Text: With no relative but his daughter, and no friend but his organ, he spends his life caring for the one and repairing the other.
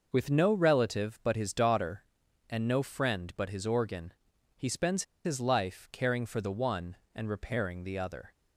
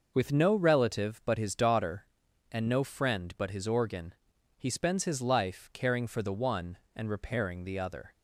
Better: second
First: pauses between "spends" and "his"; slight; at 5.0 s; 0.21 s long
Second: none

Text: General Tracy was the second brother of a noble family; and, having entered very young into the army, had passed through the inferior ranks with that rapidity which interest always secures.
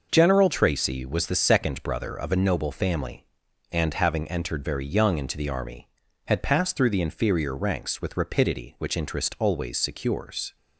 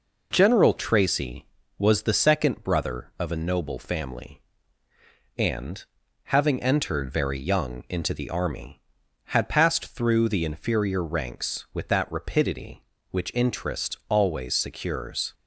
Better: second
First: skips "that"; at 8.1 s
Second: none

